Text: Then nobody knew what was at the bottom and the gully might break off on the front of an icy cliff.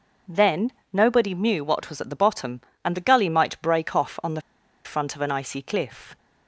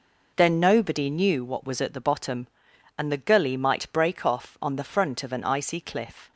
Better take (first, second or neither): second